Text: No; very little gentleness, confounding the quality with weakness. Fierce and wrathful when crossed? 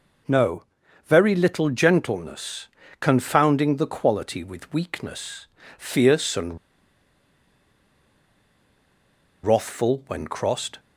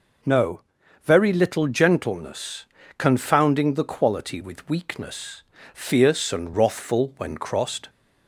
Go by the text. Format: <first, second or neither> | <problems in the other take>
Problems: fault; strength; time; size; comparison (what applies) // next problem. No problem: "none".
second | pauses between "and" and "wrathful"; strong; at 6.5 s; 2.8 s long